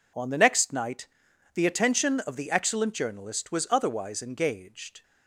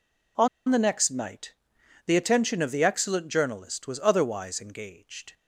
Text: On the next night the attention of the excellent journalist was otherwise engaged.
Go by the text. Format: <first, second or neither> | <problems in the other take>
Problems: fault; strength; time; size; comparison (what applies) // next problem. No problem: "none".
first | pauses between "On" and "the"; slight; at 0.4 s; 0.21 s long // pauses between "night" and "the"; noticeable; at 1.5 s; 0.52 s long; noticeable in the first